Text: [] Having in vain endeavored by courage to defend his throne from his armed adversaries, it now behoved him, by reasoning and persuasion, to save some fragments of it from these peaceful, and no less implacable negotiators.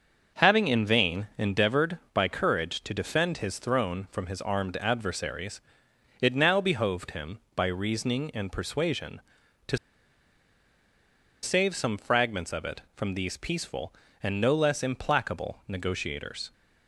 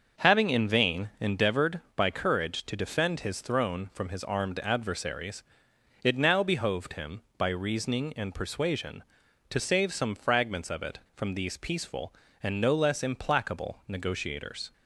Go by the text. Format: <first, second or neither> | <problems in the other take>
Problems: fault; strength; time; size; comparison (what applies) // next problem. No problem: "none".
second | starts louder than the rest; until 1.4 s; 6.5 dB; also in the second // pauses between "to" and "save"; strong; at 9.7 s; 1.6 s long